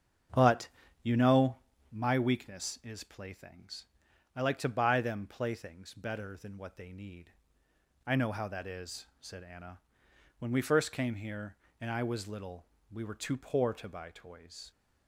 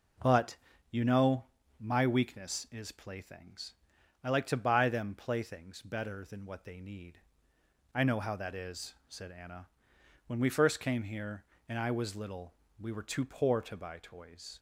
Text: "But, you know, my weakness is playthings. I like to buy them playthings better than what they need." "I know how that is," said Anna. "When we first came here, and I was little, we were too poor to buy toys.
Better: second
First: starts louder than the rest; strong; until 2.1 s; 7.5 dB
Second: none

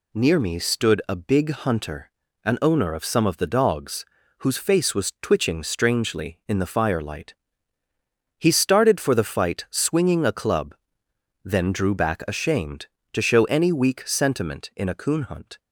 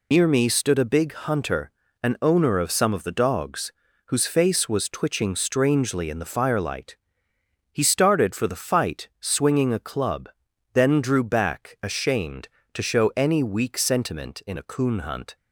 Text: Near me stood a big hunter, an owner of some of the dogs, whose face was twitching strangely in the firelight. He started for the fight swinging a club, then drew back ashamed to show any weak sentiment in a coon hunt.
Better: first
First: none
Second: loses the start of "Near"; at 0.1 s; 70 ms

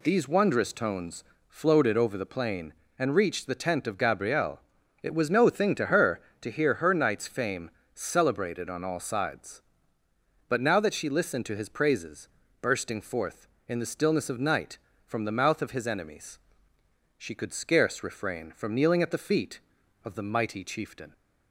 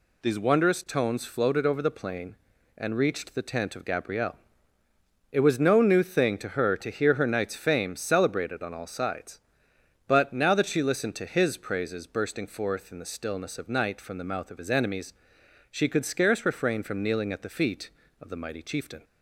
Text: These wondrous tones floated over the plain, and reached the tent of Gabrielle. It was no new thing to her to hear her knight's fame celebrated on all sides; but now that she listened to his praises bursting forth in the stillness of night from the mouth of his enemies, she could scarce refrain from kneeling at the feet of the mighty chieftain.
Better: second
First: pauses between "tones" and "floated"; slight; at 1.2 s; 0.24 s long // skips "new"; at 5.4 s // pauses between "fame" and "celebrated"; slight; at 7.6 s; 0.24 s long // pauses between "praises" and "bursting"; slight; at 12.2 s; 0.34 s long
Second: none

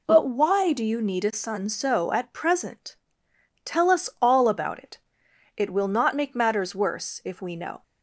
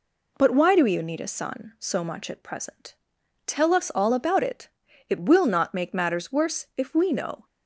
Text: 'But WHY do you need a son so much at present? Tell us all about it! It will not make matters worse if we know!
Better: second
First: skips "much"; at 2.1 s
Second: none

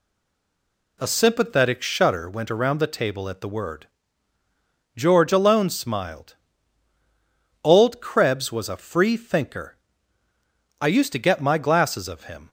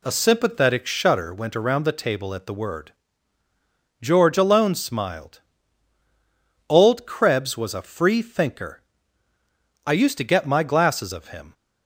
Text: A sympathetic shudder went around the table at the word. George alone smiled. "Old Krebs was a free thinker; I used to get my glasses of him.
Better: second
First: stays silent before the first word; until 1.0 s; 1.0 s long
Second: none

